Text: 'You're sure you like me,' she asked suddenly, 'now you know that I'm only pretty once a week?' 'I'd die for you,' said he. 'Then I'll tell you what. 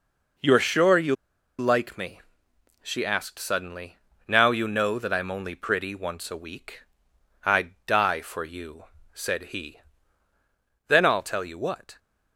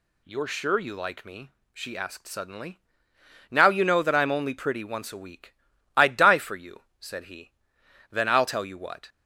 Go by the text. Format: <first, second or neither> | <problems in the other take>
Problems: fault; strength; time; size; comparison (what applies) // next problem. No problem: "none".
second | pauses between "you" and "like"; at 1.1 s; 0.44 s long